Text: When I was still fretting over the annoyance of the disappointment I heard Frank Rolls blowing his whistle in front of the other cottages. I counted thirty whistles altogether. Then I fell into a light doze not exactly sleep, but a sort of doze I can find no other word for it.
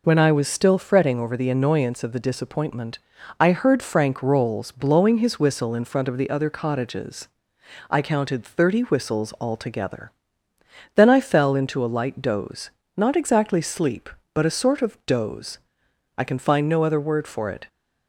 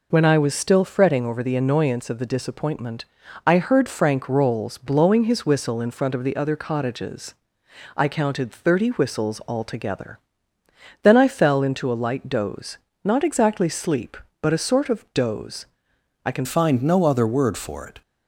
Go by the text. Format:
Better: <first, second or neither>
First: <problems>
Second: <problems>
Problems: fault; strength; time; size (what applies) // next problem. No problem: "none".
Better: first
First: pauses between "disappointment" and "I"; at 2.9 s; 0.42 s long // pauses between "doze" and "not"; slight; at 12.6 s; 0.28 s long // pauses between "doze" and "I"; noticeable; at 15.5 s; 0.60 s long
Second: pauses between "disappointment" and "I"; at 3.0 s; 0.42 s long // pauses between "doze" and "not"; slight; at 12.7 s; 0.28 s long // pauses between "doze" and "I"; noticeable; at 15.6 s; 0.60 s long // changes voice at "find"; from 16.4 s on; 1.6 s long